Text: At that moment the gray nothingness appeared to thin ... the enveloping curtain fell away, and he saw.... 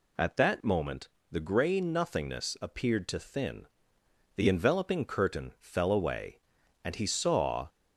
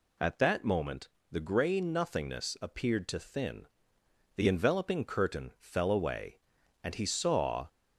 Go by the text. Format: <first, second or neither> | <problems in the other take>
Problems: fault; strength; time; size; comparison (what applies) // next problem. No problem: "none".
neither | pauses between "moment" and "the"; slight; the same in both